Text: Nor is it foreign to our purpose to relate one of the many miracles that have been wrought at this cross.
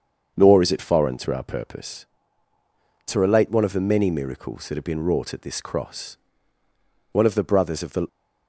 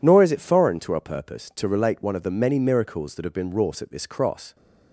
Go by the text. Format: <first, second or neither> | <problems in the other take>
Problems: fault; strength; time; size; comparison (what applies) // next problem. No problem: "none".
second | starts louder than the rest; until 1.3 s; 7 dB // goes on to say "One of the brothers of the"; noticeable; from 7.1 s on; 0.96 s long